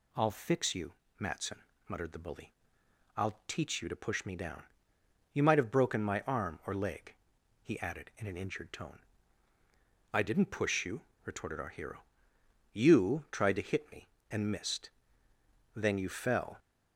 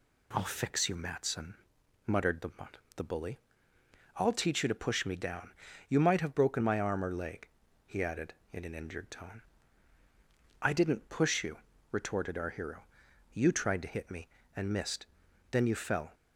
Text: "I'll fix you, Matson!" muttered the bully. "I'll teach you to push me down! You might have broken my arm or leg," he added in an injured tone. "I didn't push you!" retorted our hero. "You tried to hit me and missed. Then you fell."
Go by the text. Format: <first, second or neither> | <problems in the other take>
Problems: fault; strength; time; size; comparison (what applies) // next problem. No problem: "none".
first | says "the" twice; at 2.9 s